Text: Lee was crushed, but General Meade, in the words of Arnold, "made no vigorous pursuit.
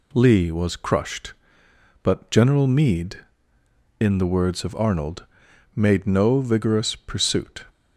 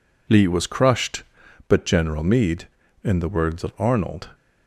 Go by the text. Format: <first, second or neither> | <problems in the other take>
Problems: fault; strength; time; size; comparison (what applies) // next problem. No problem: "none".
first | stops before "made no vigorous pursuit"; at 4.3 s